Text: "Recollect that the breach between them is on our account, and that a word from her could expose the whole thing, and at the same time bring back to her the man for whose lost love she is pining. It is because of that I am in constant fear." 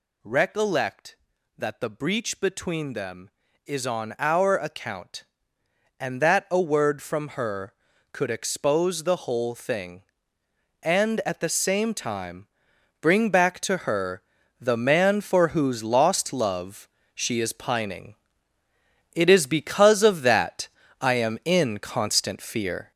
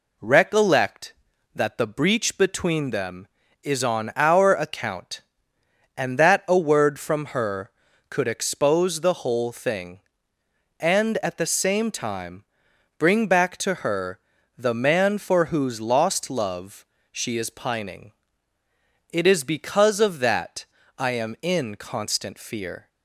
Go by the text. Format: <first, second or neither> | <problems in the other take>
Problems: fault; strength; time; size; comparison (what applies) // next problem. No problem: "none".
second | gets louder; throughout; 6.5 dB // pauses between "time" and "bring"; noticeable; at 12.4 s; 0.54 s long; noticeable in the second // pauses between "her" and "the"; at 14.2 s; 0.38 s long; also in the second // pauses between "love" and "she"; slight; at 16.8 s; 0.28 s long; slight in the second // pauses between "that" and "I"; slight; at 20.6 s; 0.34 s long; slight in the second